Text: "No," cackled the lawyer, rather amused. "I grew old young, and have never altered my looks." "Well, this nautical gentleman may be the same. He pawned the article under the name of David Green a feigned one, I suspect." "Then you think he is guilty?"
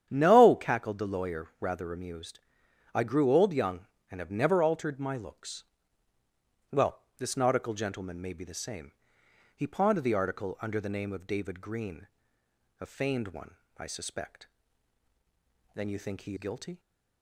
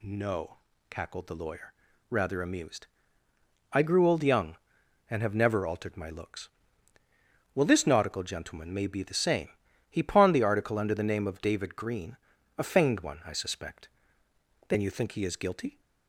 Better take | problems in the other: second | starts louder than the rest; strong; until 1.1 s; 9.5 dB // pauses between "Green" and "a"; noticeable; at 12.0 s; 0.74 s long; also in the second // skips "is"; at 16.3 s

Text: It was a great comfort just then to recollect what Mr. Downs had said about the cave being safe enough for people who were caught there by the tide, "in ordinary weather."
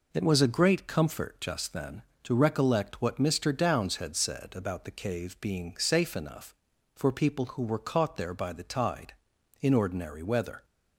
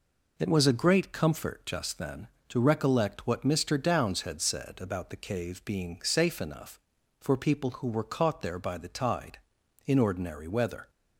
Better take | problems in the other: neither | none

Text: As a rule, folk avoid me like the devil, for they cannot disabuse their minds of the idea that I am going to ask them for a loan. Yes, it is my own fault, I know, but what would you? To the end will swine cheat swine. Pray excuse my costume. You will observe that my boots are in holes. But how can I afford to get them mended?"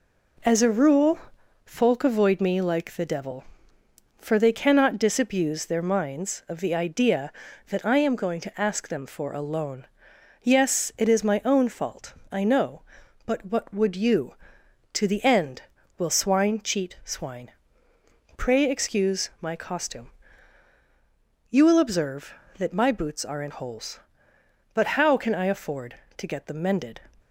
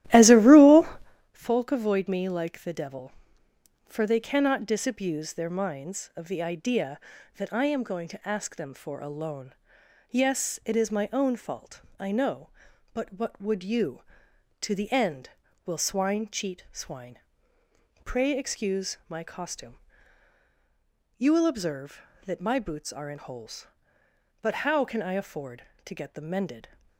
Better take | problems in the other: first | starts louder than the rest; strong; until 1.3 s; 14 dB

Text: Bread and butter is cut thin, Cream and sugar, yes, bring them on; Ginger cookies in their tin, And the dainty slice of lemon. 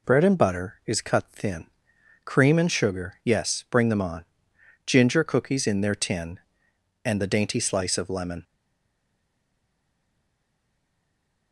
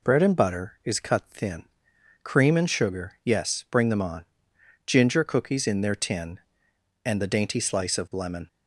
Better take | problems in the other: second | stays silent after the last word; strong; from 8.4 s on; 3.1 s long

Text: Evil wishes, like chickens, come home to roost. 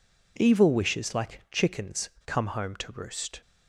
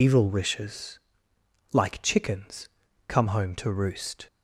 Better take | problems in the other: first | loses the start of "Evil"; at 0.0 s; 105 ms

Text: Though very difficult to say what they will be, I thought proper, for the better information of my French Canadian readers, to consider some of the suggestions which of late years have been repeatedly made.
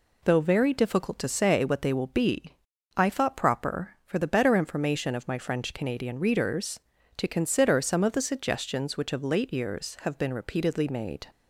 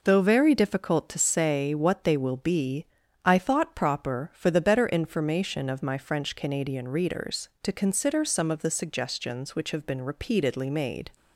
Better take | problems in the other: first | skips "of late years"; at 9.7 s

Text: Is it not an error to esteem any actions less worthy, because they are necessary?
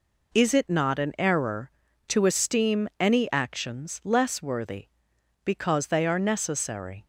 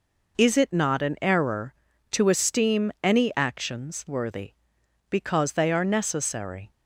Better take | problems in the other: first | skips "less"; at 4.0 s

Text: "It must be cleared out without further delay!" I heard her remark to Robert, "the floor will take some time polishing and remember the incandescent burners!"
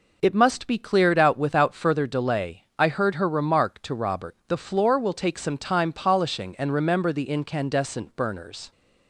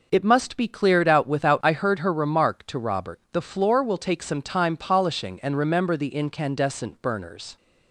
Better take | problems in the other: first | skips "further delay"; at 1.6 s

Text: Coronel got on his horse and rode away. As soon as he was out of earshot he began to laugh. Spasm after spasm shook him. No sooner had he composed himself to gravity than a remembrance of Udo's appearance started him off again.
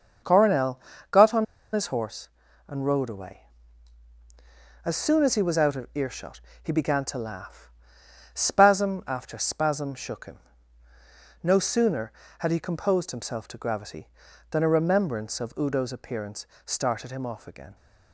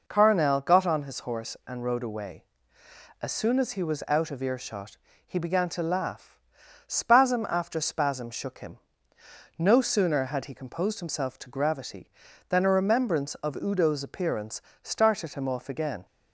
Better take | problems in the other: second | starts louder than the rest; until 1.8 s; 6.5 dB // pauses between "Coronel" and "got"; slight; at 0.7 s; 0.32 s long // pauses between "on" and "his"; slight; at 1.4 s; 0.27 s long // pauses between "earshot" and "he"; slight; at 6.4 s; 0.22 s long; slight in the second // pauses between "appearance" and "started"; slight; at 16.4 s; 0.20 s long; slight in the second

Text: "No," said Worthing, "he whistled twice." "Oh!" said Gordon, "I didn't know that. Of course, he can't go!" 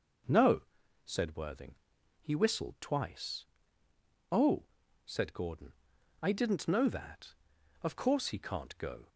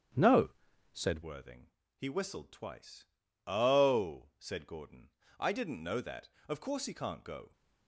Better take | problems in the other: first | starts louder than the rest; strong; until 1.6 s; 8.5 dB // changes voice at "Worthing"; from 1.2 s on; 6.3 s long

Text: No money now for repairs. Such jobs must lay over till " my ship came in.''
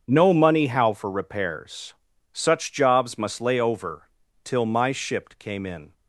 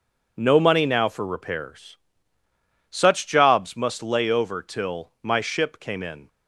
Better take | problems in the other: second | starts louder than the rest; strong; until 1.0 s; 7 dB // says "how" for "now"; at 0.6 s // pauses between "over" and "till"; slight; at 4.0 s; 0.34 s long

